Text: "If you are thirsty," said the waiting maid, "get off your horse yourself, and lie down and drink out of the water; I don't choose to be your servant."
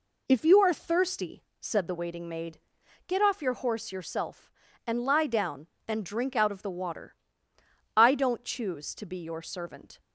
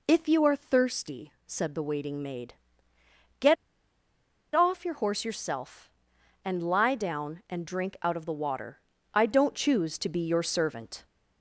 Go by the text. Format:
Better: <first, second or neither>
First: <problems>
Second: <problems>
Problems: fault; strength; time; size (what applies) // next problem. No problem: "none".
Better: first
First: none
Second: pauses between "get" and "off"; at 3.5 s; 0.99 s long